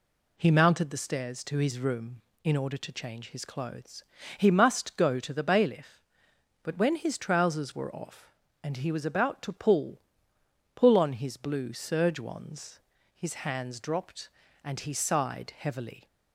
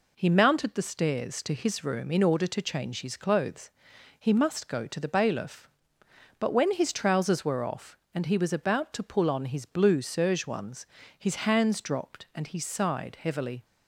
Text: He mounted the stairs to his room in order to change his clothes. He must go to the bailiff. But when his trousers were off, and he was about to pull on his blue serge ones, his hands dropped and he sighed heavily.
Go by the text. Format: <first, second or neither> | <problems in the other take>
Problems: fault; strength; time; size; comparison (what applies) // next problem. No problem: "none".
second | says "pull" twice; at 10.7 s